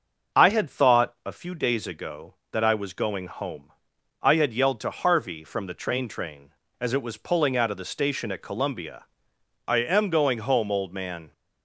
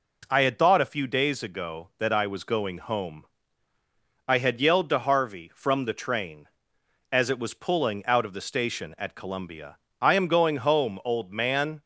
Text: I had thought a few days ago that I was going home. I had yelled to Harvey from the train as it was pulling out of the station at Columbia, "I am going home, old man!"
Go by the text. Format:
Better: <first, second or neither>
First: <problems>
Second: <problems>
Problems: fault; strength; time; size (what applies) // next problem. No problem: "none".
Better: second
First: starts louder than the rest; until 1.4 s; 6 dB // says "train" twice; at 6.0 s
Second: none